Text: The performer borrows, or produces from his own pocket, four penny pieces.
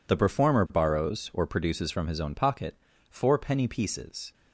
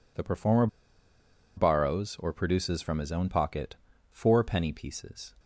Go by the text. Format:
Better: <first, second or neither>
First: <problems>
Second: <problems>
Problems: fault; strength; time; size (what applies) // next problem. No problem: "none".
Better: first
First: none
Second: pauses between "performer" and "borrows"; noticeable; at 0.6 s; 0.89 s long